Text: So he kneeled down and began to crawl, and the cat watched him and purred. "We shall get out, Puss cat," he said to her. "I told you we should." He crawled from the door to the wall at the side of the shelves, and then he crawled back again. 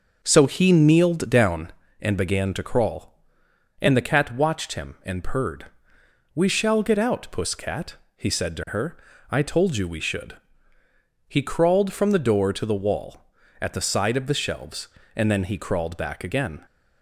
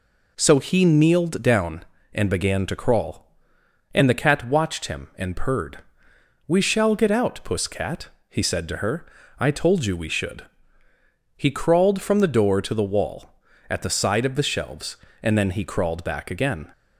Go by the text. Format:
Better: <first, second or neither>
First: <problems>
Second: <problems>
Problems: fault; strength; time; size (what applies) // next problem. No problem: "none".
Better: second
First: starts louder than the rest; noticeable; until 2.0 s; 5.5 dB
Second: none